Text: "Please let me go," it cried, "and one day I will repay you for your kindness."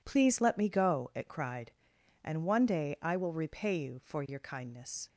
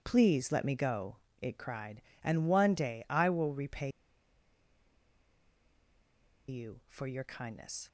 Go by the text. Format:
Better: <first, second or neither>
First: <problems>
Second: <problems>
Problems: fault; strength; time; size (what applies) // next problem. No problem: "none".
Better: first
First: none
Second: pauses between "repay" and "you"; strong; at 3.8 s; 2.5 s long